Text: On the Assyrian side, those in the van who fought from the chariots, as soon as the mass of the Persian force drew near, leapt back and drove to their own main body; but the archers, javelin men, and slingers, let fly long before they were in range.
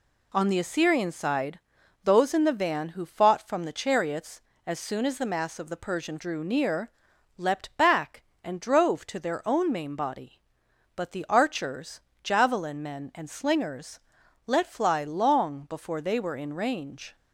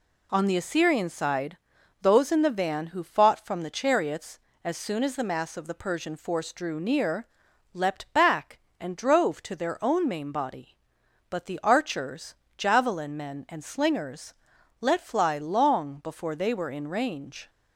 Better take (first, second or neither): second